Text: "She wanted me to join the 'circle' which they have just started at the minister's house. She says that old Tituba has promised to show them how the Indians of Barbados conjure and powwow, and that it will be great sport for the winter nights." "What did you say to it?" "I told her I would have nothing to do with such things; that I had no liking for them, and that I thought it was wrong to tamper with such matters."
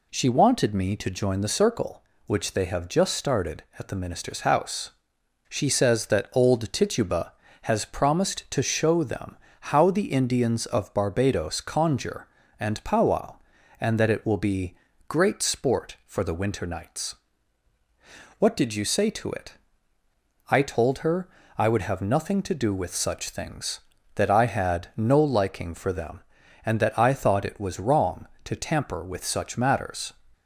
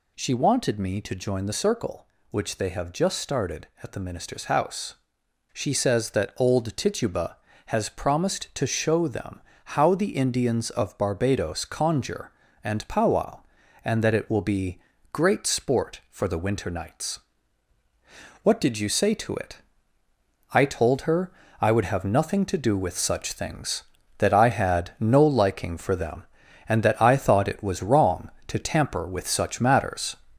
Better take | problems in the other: first | gets louder; noticeable; throughout; 4 dB // pauses between "them" and "how"; slight; at 9.4 s; 0.24 s long; slight in the first // pauses between "be" and "great"; slight; at 14.7 s; 0.32 s long; slight in the first // pauses between "her" and "I"; slight; at 21.3 s; 0.26 s long; slight in the first

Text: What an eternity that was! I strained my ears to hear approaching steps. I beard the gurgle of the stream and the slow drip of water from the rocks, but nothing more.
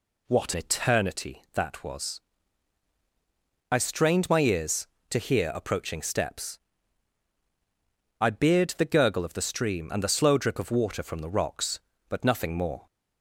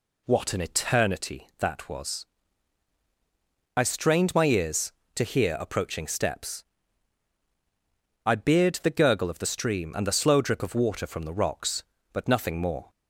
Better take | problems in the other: second | skips "an"; at 0.5 s

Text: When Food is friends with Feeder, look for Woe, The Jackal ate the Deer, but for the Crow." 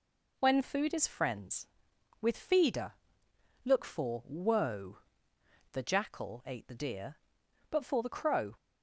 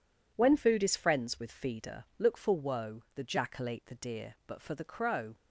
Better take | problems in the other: neither | none

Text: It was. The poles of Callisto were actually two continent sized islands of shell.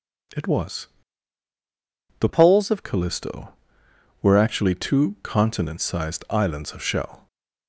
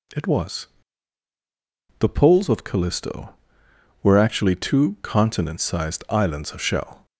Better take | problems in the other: second | changes voice from "poles" to "of"; from 2.2 to 2.8 s; 0.6 s long

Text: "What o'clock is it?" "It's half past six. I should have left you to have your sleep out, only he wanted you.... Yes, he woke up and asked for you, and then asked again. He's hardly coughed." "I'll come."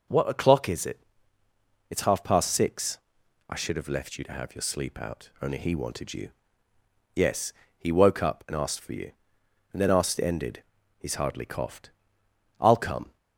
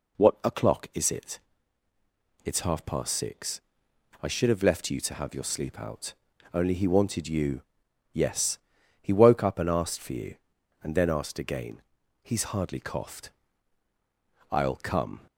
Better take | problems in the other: second | says "ended" for "again"; at 10.1 s

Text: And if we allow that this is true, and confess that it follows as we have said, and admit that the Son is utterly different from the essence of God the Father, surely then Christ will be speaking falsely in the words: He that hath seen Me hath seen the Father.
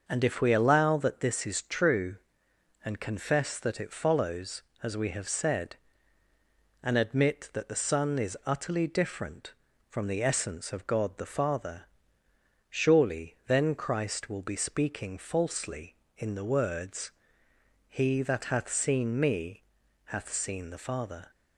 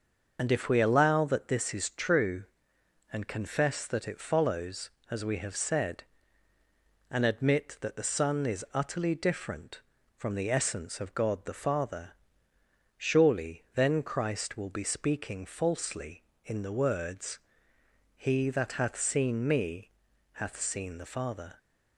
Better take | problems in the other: first | loses the start of "And"; at 0.3 s; 35 ms // starts louder than the rest; until 1.4 s; 6 dB; also in the first // pauses between "Me" and "hath"; at 19.8 s; 0.44 s long; also in the first

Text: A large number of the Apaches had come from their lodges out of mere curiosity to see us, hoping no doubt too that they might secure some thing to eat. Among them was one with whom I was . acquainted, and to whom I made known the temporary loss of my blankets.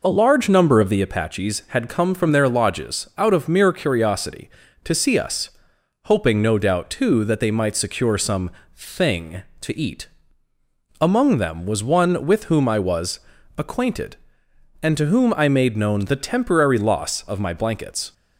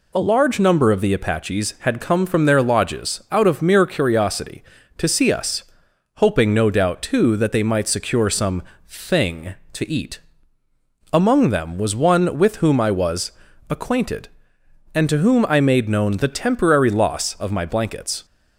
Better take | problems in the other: second | starts louder than the rest; noticeable; until 1.0 s; 4.5 dB // pauses between "some" and "thing"; slight; at 8.4 s; 0.24 s long; slight in the second

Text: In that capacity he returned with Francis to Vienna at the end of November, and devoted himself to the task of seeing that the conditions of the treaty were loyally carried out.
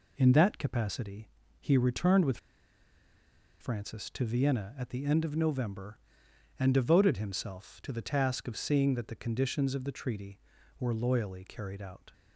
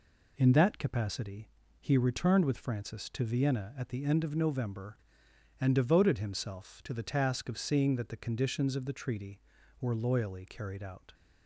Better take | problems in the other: second | pauses between "capacity" and "he"; slight; at 1.2 s; 0.30 s long; slight in the second // pauses between "with" and "Francis"; at 2.3 s; 1.2 s long

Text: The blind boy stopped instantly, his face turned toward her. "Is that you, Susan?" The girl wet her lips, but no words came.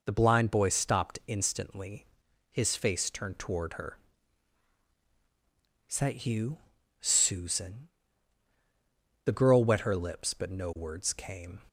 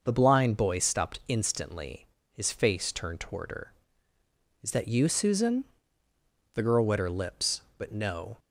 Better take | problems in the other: first | stops before "words came"; at 8.3 s

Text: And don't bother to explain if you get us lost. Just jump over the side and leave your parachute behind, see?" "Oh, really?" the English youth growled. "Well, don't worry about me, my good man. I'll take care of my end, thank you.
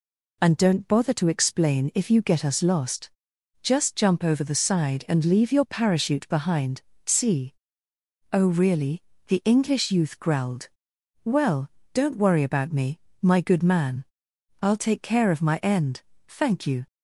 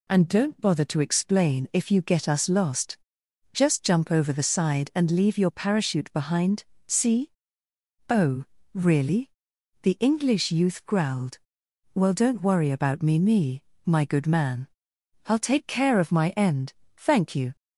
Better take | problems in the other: first | says "me" twice; at 13.1 s

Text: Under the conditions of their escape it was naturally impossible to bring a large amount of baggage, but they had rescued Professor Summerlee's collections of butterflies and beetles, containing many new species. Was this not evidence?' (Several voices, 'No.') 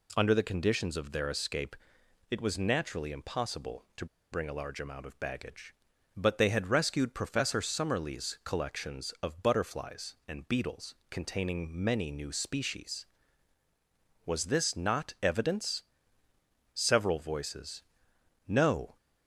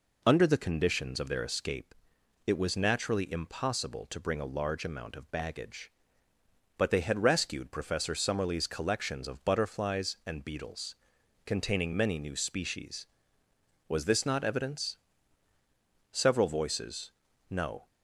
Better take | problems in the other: second | pauses between "escape" and "it"; noticeable; at 1.7 s; 0.54 s long; noticeable in the second // pauses between "to" and "bring"; slight; at 4.0 s; 0.27 s long

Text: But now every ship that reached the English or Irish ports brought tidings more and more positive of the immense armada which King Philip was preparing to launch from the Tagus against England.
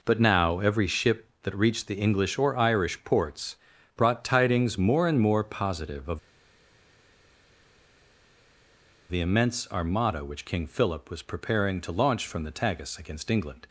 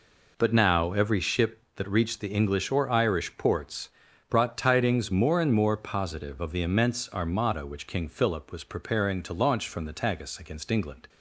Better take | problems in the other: second | pauses between "ports" and "brought"; at 3.5 s; 0.40 s long; also in the second // pauses between "of" and "the"; strong; at 6.1 s; 2.9 s long

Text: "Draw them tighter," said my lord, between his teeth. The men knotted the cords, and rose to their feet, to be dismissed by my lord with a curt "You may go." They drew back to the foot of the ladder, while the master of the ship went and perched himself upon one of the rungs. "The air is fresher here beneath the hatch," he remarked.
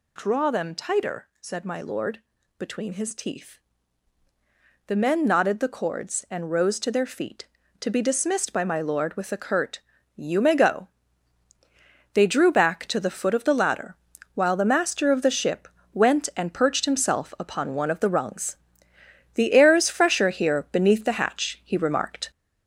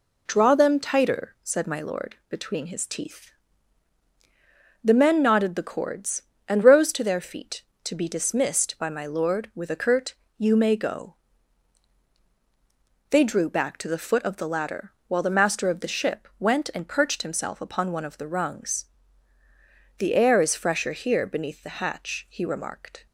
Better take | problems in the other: second | gets louder; noticeable; throughout; 5 dB // pauses between "curt" and "You"; slight; at 9.8 s; 0.34 s long; slight in the second // pauses between "ship" and "went"; slight; at 15.6 s; 0.24 s long

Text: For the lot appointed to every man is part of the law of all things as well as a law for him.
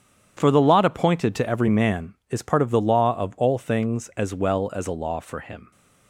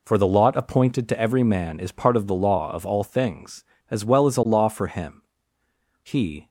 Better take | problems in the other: first | goes on to say "He"; slight; from 6.0 s on; 0.46 s long

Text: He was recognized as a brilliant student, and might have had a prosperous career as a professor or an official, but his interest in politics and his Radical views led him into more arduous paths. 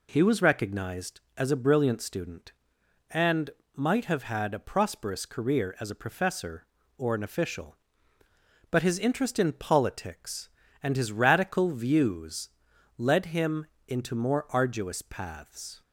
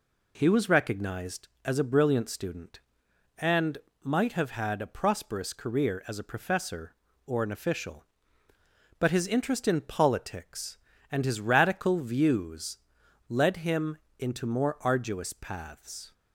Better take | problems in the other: neither | pauses between "and" and "might"; slight; the same in both // pauses between "views" and "led"; noticeable; the same in both // pauses between "him" and "into"; slight; the same in both

